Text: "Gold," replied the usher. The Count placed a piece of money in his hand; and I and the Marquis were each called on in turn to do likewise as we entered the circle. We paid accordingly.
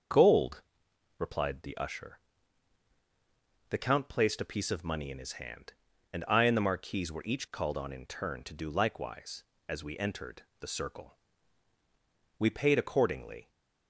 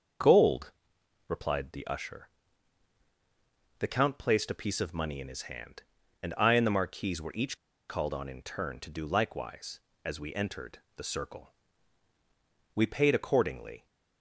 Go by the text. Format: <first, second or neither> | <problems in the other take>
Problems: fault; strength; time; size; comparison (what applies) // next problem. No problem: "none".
first | starts louder than the rest; until 1.7 s; 6.5 dB; also in the first // pauses between "each" and "called"; slight; at 7.5 s; 0.31 s long // pauses between "entered" and "the"; slight; at 10.8 s; 0.16 s long; slight in the first